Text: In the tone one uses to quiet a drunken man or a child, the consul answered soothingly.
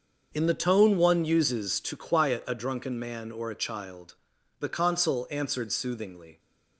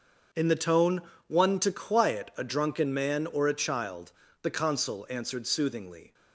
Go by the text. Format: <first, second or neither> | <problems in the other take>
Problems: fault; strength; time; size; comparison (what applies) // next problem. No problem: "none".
first | starts louder than the rest; until 1.6 s; 6.5 dB; also in the first // pauses between "tone" and "one"; slight; at 1.0 s; 0.26 s long // skips "uses"; at 1.5 s